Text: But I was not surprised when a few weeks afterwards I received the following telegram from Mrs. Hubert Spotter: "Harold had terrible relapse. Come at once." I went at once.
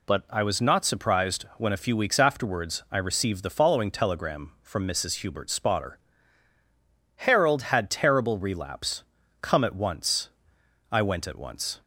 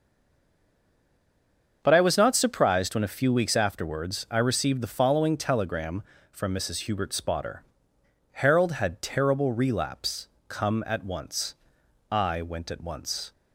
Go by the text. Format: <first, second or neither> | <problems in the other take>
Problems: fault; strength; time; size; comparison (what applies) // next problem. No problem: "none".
first | stays silent before the first word; noticeable; until 1.8 s; 1.8 s long // starts louder than the rest; until 2.8 s; 7 dB